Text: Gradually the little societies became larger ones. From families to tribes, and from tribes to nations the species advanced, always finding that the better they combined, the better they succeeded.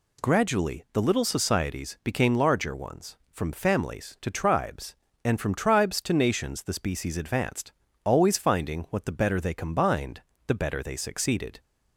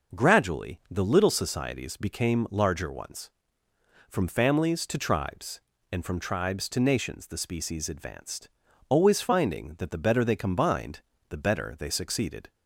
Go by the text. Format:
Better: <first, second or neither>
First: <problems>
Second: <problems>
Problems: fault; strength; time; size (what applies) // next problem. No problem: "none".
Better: second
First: says "what" for "that"; at 8.8 s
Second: none